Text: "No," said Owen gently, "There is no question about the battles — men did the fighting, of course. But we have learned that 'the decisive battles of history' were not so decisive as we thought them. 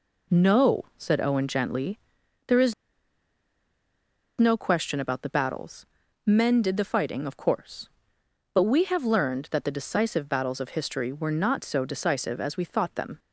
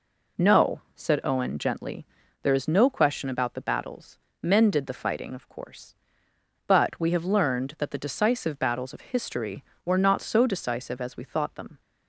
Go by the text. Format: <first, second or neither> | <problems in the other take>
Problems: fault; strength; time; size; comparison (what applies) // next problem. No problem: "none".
second | pauses between "is" and "no"; strong; at 2.7 s; 1.6 s long